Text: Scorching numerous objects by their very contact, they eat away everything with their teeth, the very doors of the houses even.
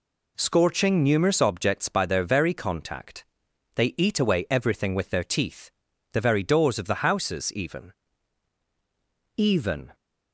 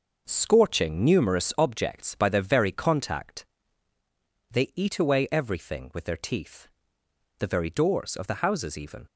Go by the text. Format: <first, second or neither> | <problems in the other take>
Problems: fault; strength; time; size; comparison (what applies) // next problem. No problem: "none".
second | says "even" twice; at 9.3 s